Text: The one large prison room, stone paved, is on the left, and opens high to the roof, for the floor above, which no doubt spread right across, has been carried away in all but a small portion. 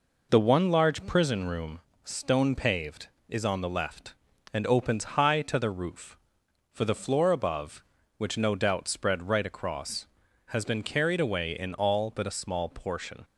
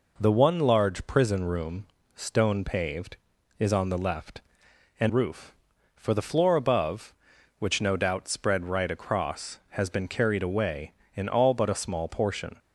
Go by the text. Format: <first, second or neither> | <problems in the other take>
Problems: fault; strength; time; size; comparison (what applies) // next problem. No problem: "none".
first | skips "opens high to the"; at 5.0 s